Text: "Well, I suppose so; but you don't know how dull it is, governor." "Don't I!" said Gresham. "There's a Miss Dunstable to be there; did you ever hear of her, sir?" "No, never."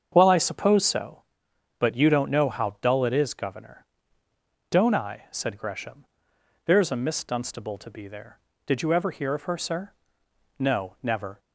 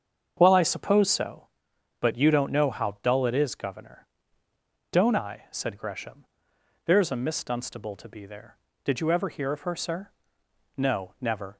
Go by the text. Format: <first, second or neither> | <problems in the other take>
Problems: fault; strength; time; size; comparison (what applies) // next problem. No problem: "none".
neither | starts louder than the rest; strong; the same in both